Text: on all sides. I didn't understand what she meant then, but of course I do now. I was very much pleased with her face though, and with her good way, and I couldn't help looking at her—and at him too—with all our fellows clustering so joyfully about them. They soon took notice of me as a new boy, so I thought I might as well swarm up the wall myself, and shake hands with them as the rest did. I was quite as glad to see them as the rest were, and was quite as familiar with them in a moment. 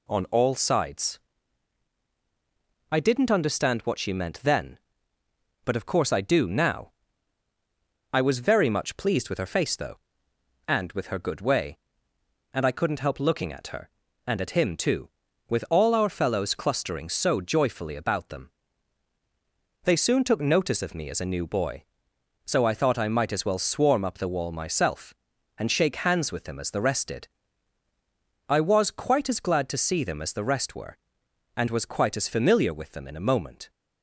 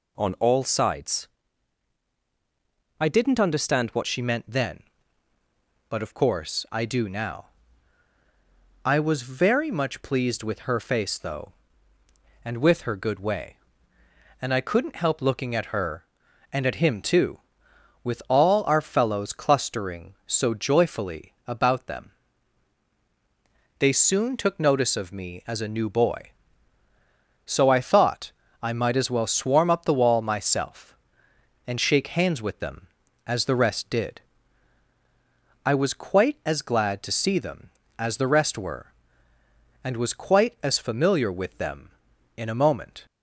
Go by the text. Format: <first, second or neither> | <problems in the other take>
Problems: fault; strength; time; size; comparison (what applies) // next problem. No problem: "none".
first | changes voice at "she"; from 4.0 s on; 39.0 s long // pauses between "thought" and "I"; slight; at 28.3 s; 0.30 s long